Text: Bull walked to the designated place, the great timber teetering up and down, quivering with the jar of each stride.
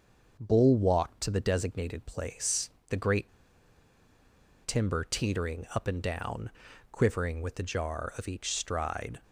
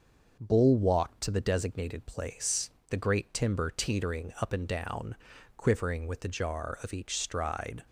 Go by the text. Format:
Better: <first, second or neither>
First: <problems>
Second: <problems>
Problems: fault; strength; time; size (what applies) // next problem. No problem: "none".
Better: second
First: starts louder than the rest; noticeable; until 1.4 s; 6 dB // pauses between "great" and "timber"; strong; at 3.2 s; 1.3 s long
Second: starts louder than the rest; noticeable; until 1.4 s; 6 dB